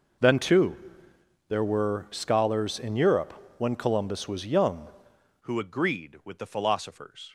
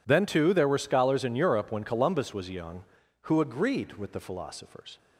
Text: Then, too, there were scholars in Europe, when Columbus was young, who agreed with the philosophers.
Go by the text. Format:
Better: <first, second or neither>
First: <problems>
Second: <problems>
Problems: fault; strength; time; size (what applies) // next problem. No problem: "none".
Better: second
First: changes voice at "who"; from 5.4 s on; 1.9 s long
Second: none